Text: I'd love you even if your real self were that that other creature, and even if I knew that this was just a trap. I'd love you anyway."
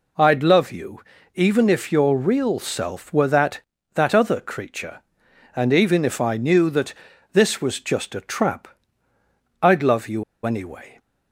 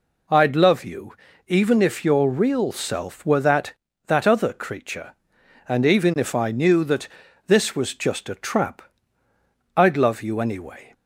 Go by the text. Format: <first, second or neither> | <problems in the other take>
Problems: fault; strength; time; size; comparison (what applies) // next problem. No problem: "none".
second | pauses between "you" and "even"; slight; at 1.0 s; 0.34 s long; slight in the second // pauses between "that" and "this"; at 6.9 s; 0.40 s long; also in the second // pauses between "you" and "anyway"; slight; at 10.2 s; 0.22 s long